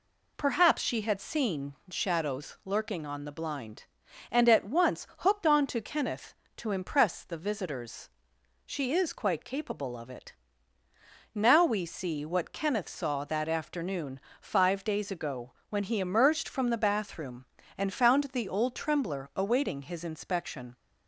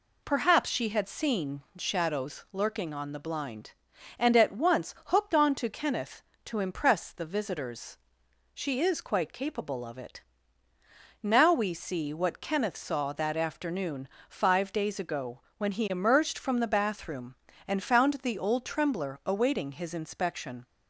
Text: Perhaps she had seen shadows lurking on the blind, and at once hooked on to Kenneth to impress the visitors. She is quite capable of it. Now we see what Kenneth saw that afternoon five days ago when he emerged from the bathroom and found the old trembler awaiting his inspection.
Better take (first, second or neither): neither